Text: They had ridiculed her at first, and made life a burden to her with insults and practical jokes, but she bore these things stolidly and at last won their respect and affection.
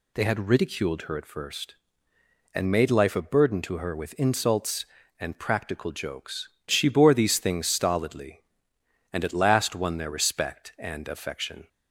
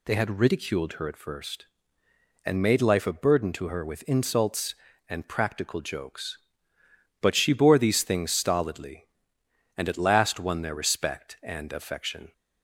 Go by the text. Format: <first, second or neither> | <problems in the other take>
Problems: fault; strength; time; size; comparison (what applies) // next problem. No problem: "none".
second | skips "but"; at 6.5 s